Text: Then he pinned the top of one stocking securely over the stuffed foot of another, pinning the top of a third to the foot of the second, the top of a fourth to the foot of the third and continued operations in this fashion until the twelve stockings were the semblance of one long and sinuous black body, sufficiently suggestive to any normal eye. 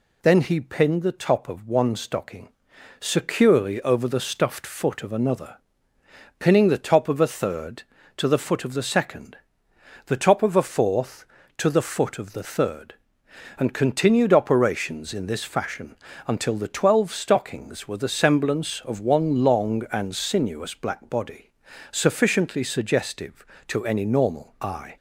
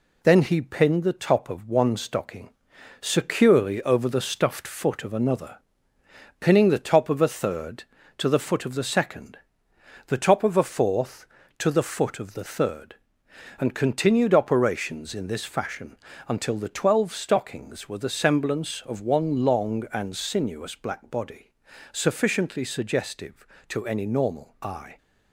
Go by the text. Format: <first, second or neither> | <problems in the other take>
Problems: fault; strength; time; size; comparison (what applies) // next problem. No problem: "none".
first | gets quieter; throughout; 3.5 dB // pauses between "stocking" and "securely"; noticeable; at 2.5 s; 0.50 s long; noticeable in the first // pauses between "fashion" and "until"; slight; at 15.9 s; 0.32 s long; slight in the first